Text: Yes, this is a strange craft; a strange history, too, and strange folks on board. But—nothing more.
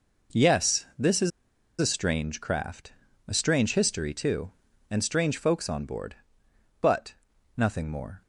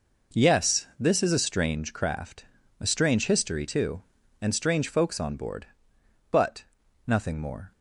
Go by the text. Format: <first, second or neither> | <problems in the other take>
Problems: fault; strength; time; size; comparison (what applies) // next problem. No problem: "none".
second | pauses between "is" and "a"; noticeable; at 1.3 s; 0.51 s long